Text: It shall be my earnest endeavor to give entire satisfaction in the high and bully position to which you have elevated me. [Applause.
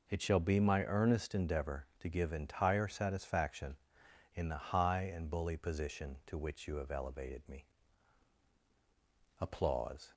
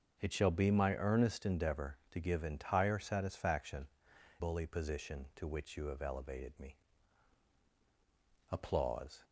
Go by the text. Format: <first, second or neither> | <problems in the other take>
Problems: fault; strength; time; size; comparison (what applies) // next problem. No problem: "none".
first | starts louder than the rest; until 1.2 s; 6.5 dB // skips "in the high and"; at 4.1 s